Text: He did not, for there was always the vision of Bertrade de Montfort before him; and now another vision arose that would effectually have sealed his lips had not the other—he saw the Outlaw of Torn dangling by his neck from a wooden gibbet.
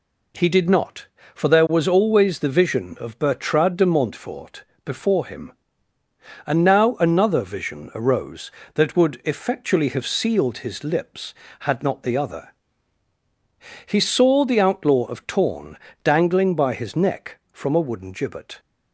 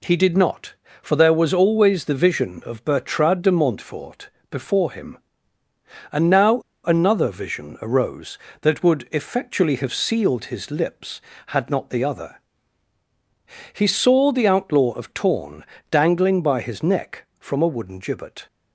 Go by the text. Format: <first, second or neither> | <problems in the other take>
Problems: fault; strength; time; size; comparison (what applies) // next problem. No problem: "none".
first | pauses between "Montfort" and "before"; slight; at 4.2 s; 0.22 s long; slight in the first // pauses between "now" and "another"; slight; at 6.6 s; 0.23 s long // pauses between "Torn" and "dangling"; slight; at 15.6 s; 0.28 s long; slight in the first